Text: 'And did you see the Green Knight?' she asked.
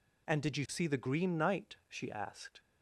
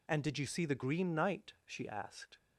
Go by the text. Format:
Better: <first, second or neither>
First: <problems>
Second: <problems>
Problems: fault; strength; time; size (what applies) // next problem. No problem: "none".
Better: neither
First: none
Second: none